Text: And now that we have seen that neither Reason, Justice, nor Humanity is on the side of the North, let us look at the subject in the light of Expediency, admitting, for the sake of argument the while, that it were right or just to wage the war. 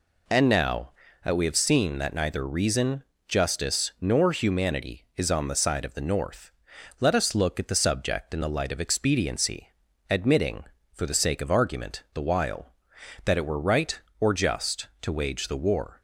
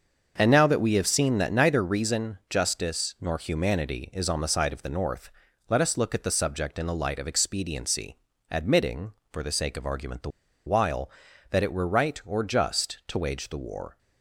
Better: first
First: none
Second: starts louder than the rest; until 1.3 s; 6.5 dB // pauses between "the" and "while"; at 10.2 s; 0.37 s long

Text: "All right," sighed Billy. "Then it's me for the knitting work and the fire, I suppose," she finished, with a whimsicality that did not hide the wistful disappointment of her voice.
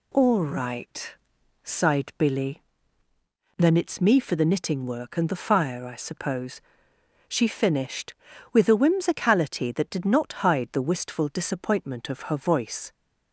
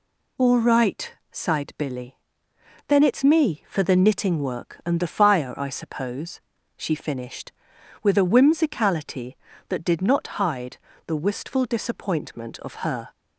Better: first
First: none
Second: pauses between "hide" and "the"; slight; at 10.7 s; 0.28 s long // stops before "voice"; at 13.1 s

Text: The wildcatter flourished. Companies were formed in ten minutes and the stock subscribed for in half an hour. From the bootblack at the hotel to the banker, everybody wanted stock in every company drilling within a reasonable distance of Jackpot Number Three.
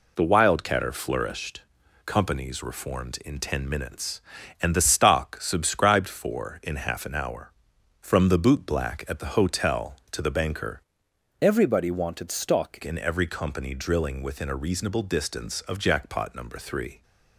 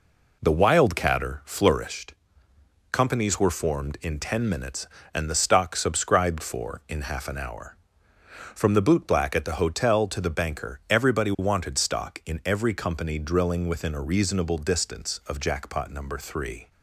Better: second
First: changes voice from "everybody" to "stock"; from 11.4 to 12.7 s; 1.3 s long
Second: none

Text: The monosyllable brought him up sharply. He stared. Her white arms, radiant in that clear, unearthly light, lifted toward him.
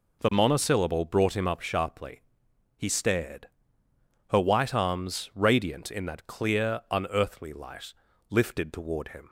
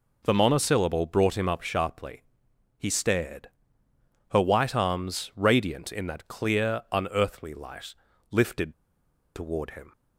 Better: first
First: none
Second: pauses between "lifted" and "toward"; noticeable; at 8.7 s; 0.62 s long

